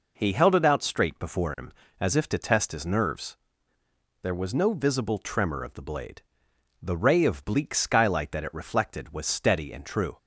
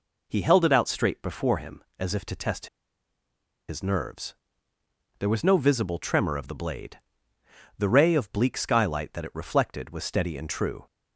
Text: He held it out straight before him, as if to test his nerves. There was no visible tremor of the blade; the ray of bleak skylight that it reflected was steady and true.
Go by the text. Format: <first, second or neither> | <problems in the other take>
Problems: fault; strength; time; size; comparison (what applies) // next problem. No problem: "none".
first | pauses between "test" and "his"; at 2.6 s; 1.0 s long